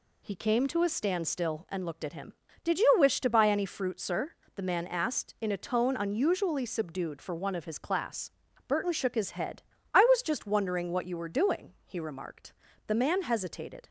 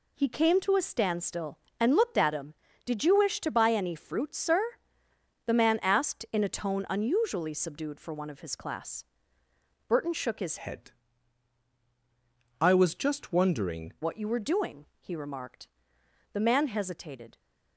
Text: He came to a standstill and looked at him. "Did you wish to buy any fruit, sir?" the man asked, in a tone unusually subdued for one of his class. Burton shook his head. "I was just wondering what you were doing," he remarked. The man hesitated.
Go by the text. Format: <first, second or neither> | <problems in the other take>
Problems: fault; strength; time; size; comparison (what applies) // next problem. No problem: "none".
first | changes voice from "head" to "wondering"; from 10.6 to 13.9 s; 3.3 s long